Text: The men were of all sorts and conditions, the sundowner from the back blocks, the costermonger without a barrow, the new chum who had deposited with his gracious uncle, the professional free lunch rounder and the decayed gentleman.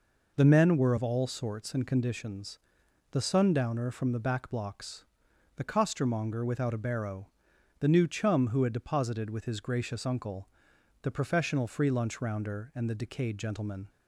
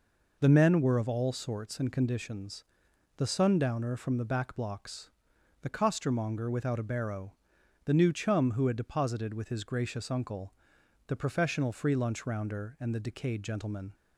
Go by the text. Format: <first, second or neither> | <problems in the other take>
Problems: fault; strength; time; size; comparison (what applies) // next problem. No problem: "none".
neither | none